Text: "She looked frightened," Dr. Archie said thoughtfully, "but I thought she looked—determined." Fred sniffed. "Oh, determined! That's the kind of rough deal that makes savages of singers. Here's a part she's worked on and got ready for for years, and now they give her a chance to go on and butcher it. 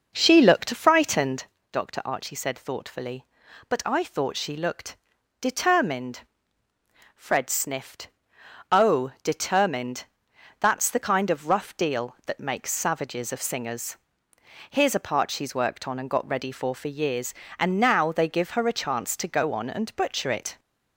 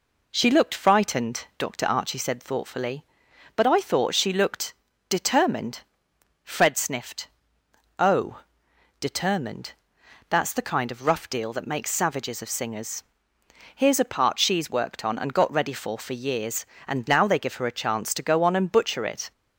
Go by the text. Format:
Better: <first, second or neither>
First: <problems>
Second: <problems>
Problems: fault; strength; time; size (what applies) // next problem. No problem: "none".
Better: second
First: starts louder than the rest; noticeable; until 1.6 s; 5.5 dB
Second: none